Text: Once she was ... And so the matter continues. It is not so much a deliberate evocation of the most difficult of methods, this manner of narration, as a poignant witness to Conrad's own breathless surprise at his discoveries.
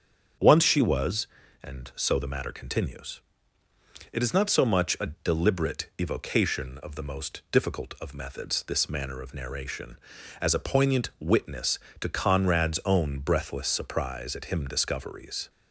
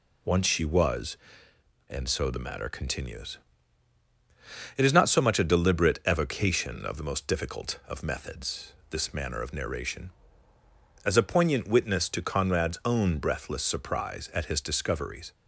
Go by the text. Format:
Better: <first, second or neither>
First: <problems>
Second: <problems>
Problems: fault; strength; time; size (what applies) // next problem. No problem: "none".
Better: second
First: starts louder than the rest; strong; until 1.7 s; 7 dB // says "him" for "his"; at 14.4 s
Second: none